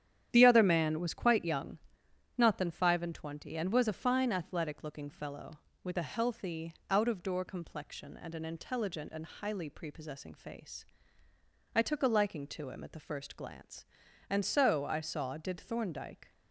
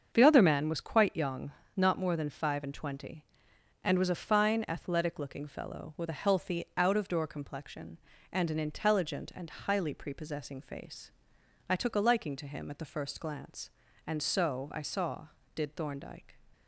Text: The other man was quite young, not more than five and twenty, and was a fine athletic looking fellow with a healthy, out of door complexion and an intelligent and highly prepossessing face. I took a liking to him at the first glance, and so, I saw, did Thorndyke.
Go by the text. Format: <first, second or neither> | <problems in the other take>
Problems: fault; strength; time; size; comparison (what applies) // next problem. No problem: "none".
second | starts louder than the rest; strong; until 1.3 s; 10 dB; also in the second // skips "more"; at 2.5 s